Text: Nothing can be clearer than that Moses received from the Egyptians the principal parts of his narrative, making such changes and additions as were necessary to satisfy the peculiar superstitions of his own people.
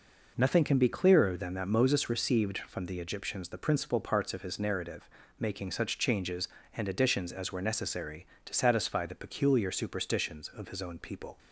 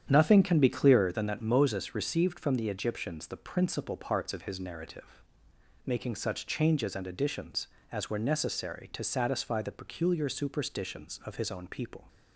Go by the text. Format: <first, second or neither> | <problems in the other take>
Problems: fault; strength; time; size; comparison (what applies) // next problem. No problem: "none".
first | starts louder than the rest; strong; until 1.2 s; 9 dB